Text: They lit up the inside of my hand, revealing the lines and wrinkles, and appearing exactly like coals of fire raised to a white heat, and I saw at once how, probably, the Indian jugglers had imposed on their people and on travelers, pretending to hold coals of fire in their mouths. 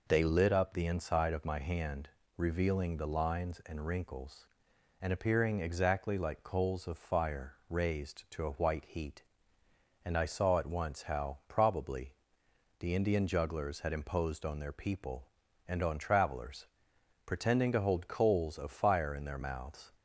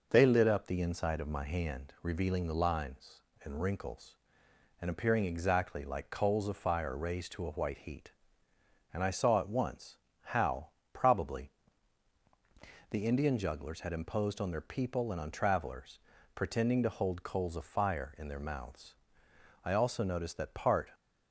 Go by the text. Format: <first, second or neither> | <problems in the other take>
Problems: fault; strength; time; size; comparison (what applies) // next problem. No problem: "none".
first | pauses between "once" and "how"; slight; at 9.9 s; 0.24 s long // goes on to say "I also noticed that part"; noticeable; from 19.6 s on; 1.2 s long